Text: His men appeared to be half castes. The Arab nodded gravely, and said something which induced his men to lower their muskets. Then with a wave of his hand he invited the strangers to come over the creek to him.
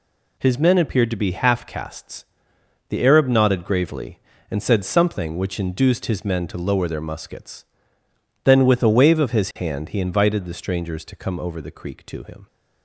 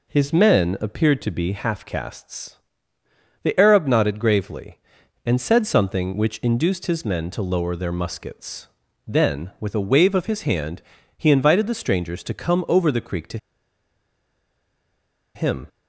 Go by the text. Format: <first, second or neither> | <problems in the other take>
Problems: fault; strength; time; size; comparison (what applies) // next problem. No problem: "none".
first | pauses between "hand" and "he"; slight; at 10.8 s; 0.34 s long // pauses between "to" and "him"; strong; at 13.3 s; 1.9 s long